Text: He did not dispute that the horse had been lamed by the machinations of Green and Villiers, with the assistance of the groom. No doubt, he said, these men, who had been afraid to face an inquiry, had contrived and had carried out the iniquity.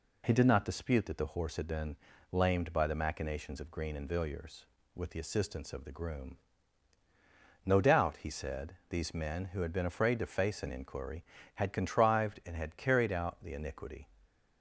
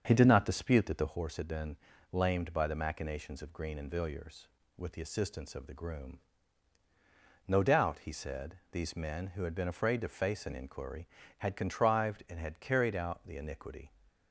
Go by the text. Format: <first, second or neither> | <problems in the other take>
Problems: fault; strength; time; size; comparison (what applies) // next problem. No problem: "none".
first | starts louder than the rest; until 1.2 s; 7 dB // pauses between "been" and "lamed"; slight; at 1.7 s; 0.34 s long; slight in the first